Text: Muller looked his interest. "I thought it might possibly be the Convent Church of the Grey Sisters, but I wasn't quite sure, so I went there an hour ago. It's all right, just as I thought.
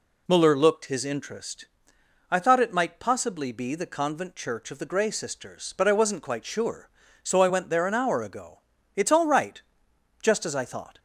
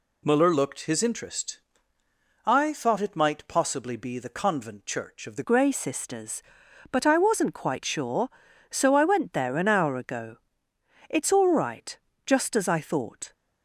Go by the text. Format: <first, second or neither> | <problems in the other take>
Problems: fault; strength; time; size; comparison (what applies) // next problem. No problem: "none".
first | changes voice at "Grey"; from 5.4 s on; 7.9 s long